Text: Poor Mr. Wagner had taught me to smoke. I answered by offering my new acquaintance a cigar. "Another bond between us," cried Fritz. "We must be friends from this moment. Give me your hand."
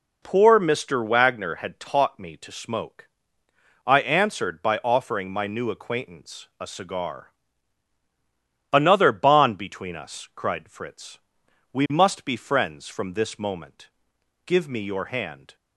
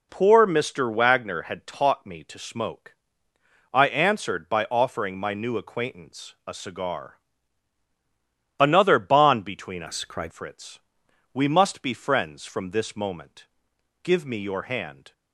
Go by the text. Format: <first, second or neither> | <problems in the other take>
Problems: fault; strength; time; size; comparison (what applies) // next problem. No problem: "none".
first | changes voice from "us" to "cried"; from 9.8 to 10.3 s; 0.5 s long